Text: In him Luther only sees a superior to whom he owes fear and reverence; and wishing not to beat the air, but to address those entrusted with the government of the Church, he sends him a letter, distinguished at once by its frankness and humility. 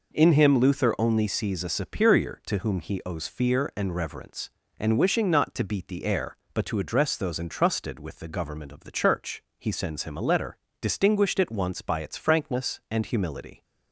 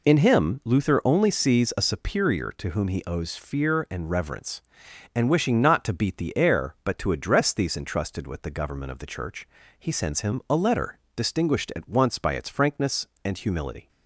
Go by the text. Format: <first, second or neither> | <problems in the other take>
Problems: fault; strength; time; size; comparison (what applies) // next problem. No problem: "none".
first | says "these" for "those"; at 7.5 s